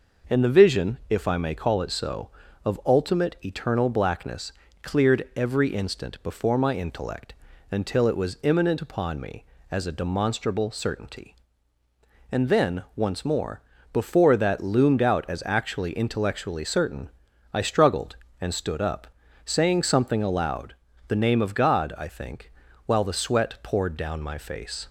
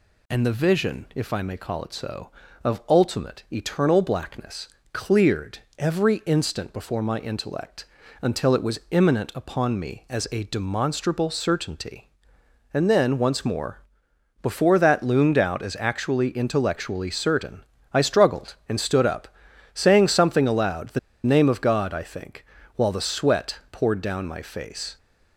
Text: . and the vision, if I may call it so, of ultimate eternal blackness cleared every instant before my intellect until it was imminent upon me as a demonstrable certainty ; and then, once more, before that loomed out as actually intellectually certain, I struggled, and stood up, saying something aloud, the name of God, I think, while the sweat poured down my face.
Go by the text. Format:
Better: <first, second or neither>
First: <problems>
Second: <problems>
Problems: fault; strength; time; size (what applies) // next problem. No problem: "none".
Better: first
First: pauses between "blackness" and "cleared"; slight; at 4.5 s; 0.30 s long // pauses between "intellect" and "until"; slight; at 7.3 s; 0.36 s long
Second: pauses between "blackness" and "cleared"; slight; at 4.6 s; 0.24 s long // pauses between "cleared" and "every"; slight; at 5.5 s; 0.20 s long // pauses between "intellect" and "until"; slight; at 7.8 s; 0.36 s long // pauses between "the" and "name"; slight; at 20.9 s; 0.25 s long